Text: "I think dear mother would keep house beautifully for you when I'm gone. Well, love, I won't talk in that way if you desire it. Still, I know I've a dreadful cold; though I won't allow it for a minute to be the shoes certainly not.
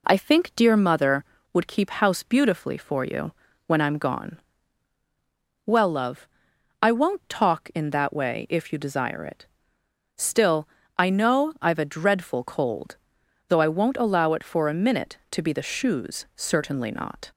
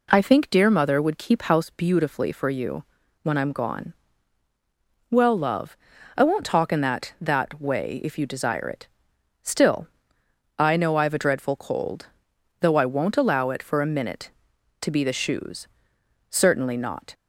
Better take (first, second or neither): first